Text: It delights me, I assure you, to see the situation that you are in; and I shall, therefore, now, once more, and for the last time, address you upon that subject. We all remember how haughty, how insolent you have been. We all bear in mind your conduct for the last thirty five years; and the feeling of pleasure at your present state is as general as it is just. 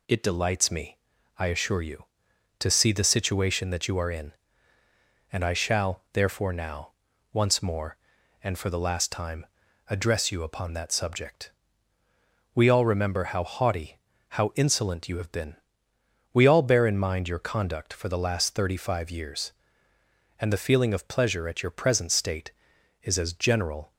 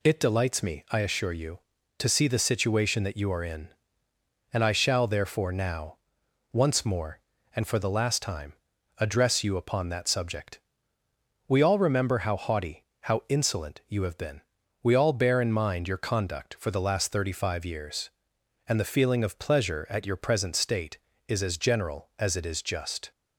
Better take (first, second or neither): second